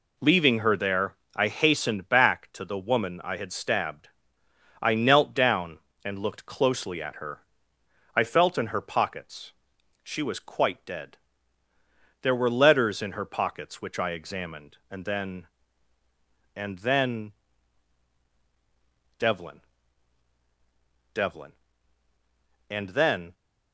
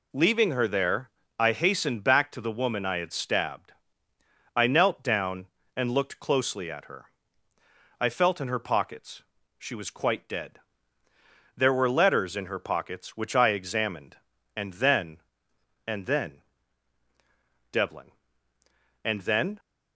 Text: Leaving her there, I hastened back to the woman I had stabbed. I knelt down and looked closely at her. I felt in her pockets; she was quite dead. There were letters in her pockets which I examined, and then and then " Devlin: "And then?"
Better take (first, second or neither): second